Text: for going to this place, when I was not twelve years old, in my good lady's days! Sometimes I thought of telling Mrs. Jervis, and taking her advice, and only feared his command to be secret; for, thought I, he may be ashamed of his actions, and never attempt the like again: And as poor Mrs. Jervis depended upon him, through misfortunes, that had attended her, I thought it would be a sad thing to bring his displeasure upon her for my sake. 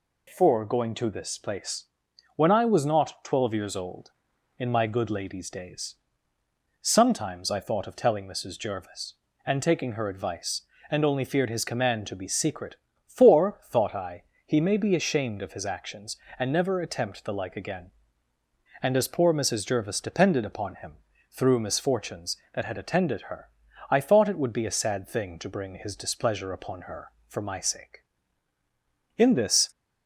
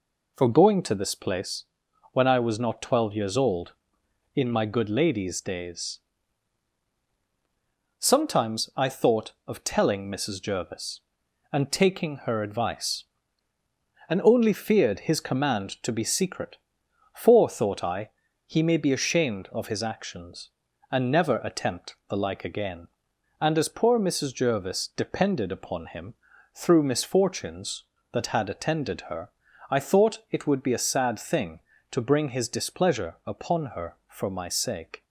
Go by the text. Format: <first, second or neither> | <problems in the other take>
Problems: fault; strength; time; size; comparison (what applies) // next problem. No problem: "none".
second | goes on to say "In this"; from 29.1 s on; 0.54 s long